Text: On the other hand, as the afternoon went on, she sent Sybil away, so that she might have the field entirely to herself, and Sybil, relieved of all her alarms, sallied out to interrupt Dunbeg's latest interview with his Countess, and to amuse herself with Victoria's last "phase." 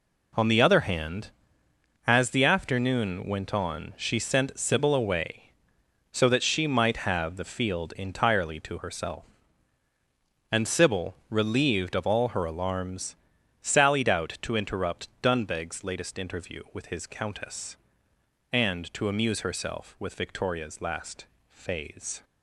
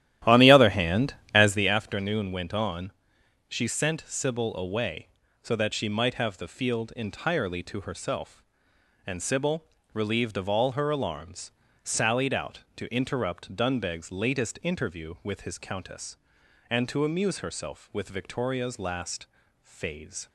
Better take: first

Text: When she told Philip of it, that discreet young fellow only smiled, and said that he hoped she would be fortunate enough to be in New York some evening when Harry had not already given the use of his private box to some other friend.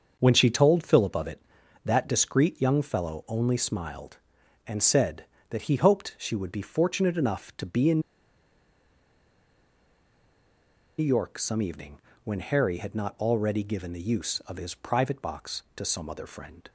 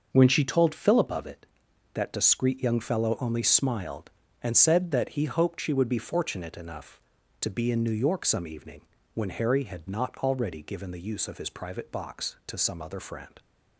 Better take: second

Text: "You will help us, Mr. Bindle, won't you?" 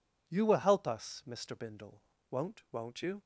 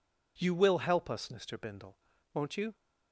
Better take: second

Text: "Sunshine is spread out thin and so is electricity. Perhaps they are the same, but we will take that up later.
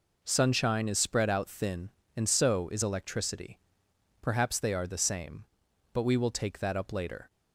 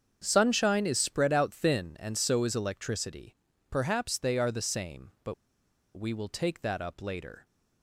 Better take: first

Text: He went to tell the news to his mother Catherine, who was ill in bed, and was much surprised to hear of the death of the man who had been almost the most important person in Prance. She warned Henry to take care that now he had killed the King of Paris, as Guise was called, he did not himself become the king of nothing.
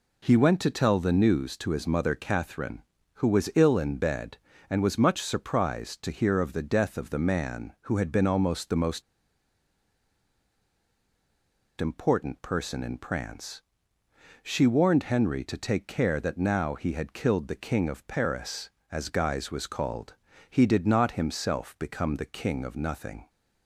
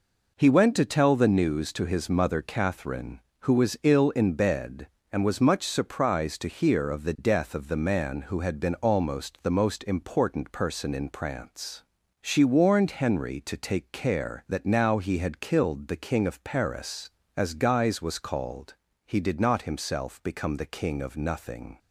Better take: second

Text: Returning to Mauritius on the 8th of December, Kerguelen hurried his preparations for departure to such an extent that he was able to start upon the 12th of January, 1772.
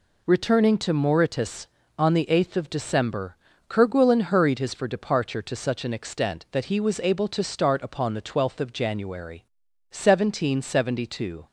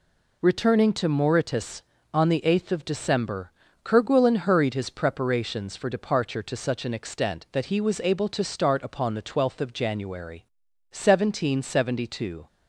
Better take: second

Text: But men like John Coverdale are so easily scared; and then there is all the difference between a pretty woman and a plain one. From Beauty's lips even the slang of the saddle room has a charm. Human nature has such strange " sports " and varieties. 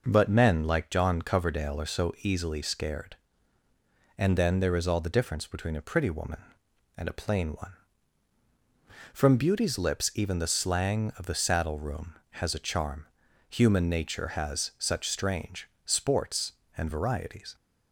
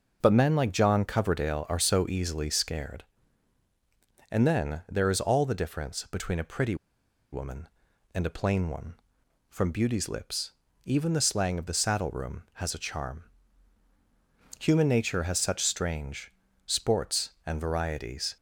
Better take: first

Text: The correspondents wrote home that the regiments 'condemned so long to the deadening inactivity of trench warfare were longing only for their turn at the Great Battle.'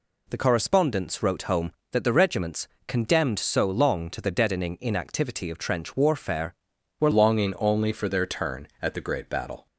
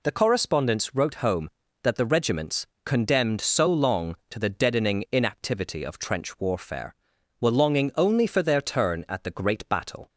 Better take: second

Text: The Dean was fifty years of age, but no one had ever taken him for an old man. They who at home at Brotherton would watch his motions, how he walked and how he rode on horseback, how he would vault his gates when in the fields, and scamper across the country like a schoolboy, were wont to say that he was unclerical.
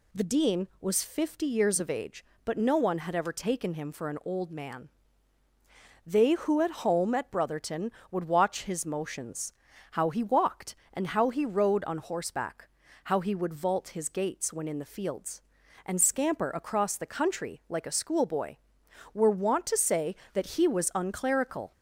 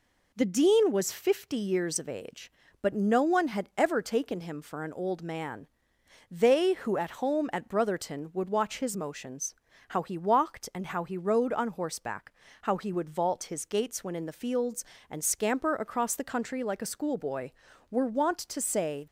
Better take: first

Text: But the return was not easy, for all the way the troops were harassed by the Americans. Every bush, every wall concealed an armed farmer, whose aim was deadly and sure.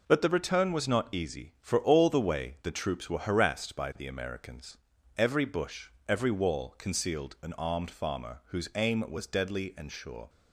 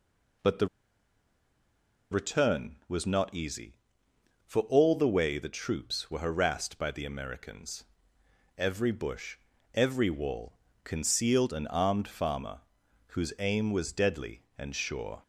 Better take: first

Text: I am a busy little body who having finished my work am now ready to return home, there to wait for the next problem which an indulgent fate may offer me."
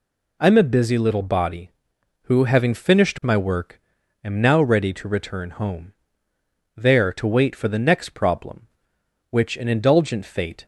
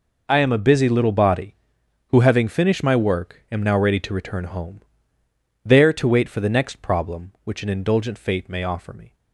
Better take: second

